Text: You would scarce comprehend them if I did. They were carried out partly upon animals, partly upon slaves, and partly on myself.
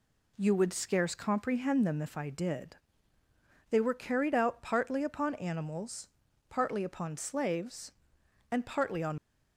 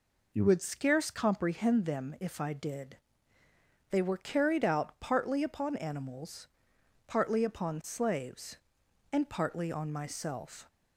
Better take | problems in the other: second | stops before "myself"; at 9.1 s

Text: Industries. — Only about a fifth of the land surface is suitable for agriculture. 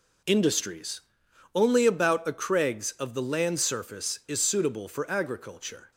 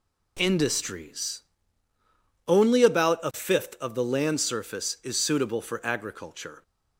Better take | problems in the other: second | says "craigs" for "fifth"; at 2.3 s

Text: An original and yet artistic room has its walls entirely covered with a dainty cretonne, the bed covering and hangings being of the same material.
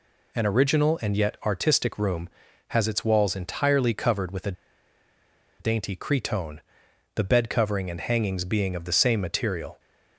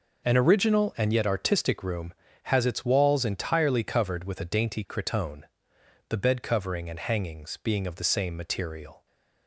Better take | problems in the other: second | pauses between "a" and "dainty"; at 4.5 s; 1.0 s long

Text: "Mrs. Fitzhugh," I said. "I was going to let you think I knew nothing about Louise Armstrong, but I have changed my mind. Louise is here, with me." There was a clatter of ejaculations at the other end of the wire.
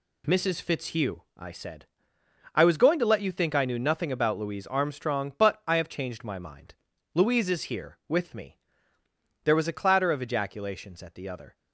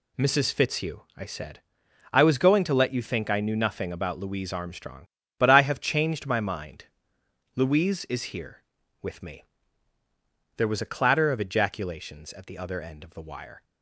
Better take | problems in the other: second | stops before "end of the wire"; at 11.5 s

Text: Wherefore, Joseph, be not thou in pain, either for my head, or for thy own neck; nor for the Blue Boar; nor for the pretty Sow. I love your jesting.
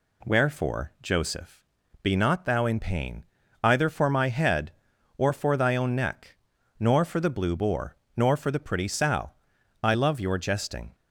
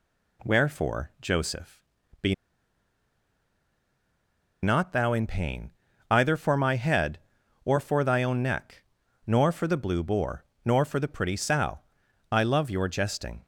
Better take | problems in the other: first | pauses between "be" and "not"; strong; at 2.3 s; 2.2 s long

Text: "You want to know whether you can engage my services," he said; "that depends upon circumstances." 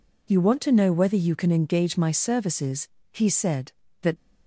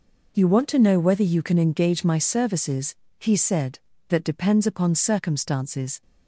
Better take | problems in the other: second | stops before "depends upon circumstances"; at 4.1 s

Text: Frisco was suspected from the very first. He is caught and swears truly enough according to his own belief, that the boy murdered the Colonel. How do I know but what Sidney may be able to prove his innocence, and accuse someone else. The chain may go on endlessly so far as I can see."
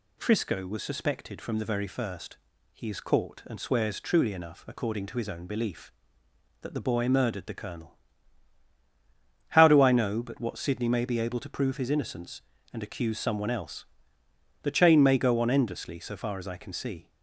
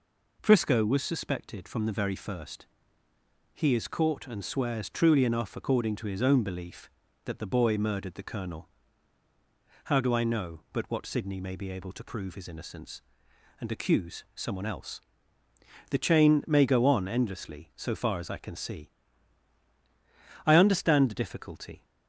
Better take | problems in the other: first | goes on to say "I understand the difficulty"; from 20.4 s on; 1.4 s long

